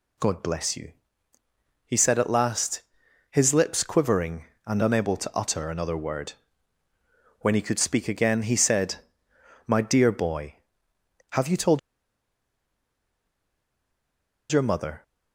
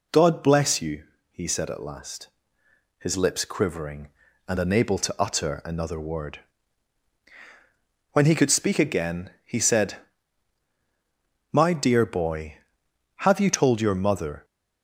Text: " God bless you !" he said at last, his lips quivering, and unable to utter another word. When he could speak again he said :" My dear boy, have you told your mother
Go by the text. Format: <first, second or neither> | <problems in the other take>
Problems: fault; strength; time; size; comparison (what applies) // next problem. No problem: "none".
second | pauses between "told" and "your"; strong; at 11.7 s; 2.7 s long